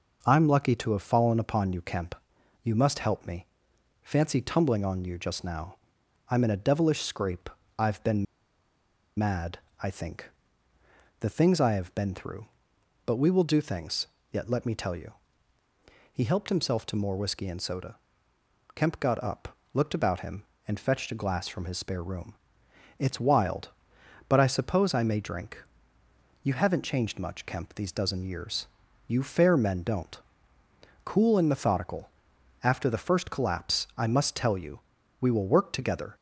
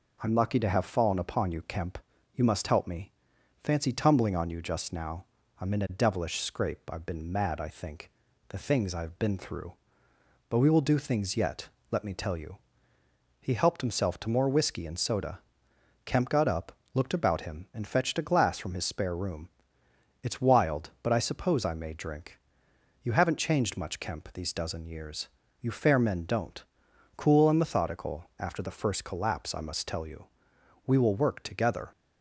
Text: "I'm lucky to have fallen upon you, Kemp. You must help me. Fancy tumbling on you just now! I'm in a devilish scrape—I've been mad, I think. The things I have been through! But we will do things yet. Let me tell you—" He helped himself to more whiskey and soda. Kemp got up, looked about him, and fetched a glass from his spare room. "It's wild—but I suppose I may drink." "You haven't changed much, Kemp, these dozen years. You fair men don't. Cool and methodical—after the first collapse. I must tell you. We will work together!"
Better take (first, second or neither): second